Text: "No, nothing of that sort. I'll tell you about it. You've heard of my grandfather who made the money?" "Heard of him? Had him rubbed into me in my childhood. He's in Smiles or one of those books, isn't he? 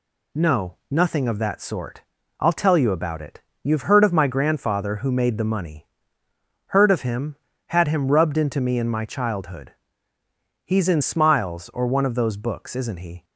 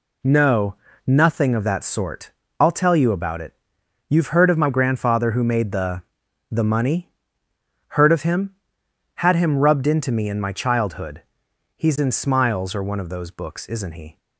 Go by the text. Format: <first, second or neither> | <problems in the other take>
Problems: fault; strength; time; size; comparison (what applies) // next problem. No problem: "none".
first | says "the" twice; at 6.5 s